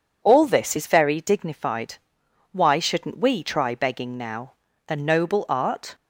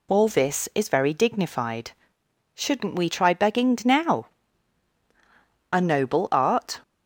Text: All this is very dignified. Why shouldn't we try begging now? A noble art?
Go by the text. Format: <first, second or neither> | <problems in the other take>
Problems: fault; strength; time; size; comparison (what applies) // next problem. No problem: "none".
first | skips "Why"; at 2.2 s